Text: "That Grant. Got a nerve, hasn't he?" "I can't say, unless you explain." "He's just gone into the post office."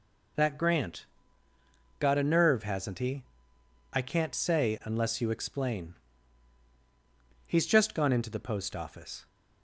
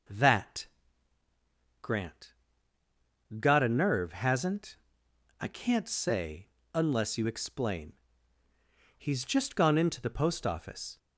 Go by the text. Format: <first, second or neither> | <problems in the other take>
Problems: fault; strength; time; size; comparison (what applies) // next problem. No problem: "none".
first | pauses between "That" and "Grant"; at 0.6 s; 1.1 s long // skips "he"; at 5.0 s